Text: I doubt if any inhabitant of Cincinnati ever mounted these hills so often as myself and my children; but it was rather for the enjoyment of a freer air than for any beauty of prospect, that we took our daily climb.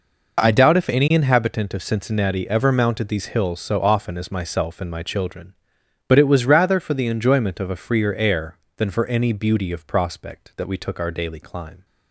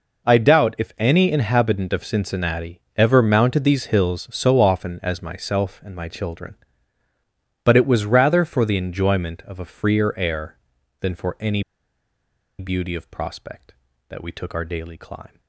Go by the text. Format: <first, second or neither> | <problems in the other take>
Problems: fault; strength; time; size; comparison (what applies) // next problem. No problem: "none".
first | pauses between "any" and "beauty"; noticeable; at 11.6 s; 0.97 s long